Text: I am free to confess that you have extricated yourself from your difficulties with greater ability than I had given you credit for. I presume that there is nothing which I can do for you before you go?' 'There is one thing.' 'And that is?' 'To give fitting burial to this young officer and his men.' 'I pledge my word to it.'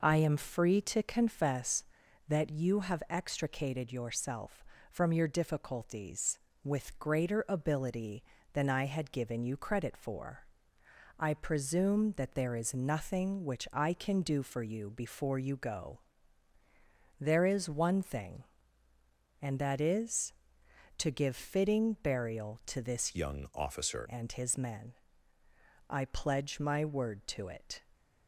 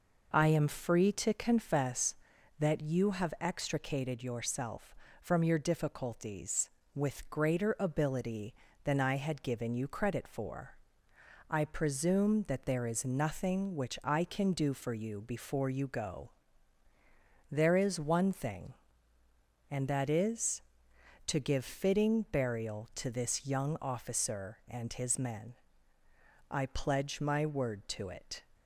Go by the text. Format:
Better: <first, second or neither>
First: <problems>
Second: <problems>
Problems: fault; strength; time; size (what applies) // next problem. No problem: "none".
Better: second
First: changes voice from "young" to "officer"; from 23.1 to 24.0 s; 0.9 s long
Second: none